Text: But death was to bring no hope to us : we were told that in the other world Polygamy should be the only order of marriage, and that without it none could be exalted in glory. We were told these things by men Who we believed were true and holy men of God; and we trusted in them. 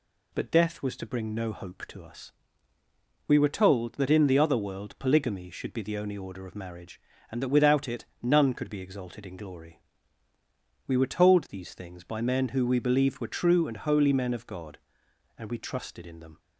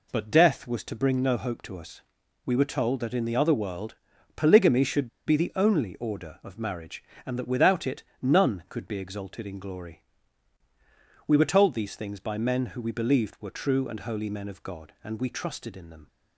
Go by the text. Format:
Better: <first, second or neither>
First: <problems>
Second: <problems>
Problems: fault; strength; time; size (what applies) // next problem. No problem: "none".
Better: first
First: none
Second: pauses between "world" and "Polygamy"; at 3.9 s; 0.40 s long // pauses between "should" and "be"; slight; at 5.0 s; 0.18 s long // pauses between "it" and "none"; slight; at 8.0 s; 0.20 s long